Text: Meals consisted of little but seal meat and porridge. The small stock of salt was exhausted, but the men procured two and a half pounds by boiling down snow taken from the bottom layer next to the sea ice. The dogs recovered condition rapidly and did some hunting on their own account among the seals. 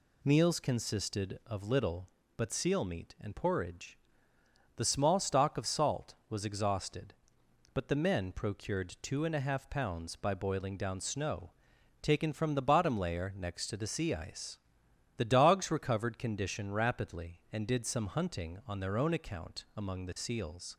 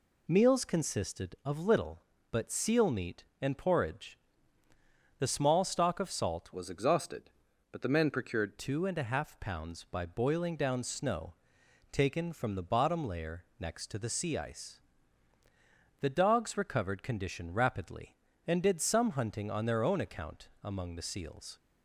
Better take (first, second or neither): first